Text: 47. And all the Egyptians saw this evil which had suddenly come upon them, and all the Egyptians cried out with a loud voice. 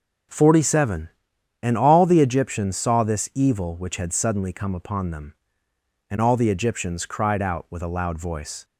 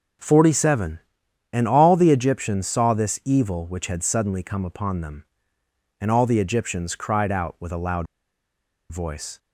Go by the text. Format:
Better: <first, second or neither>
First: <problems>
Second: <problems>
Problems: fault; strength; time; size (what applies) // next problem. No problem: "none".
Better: first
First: none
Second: pauses between "loud" and "voice"; noticeable; at 8.0 s; 0.84 s long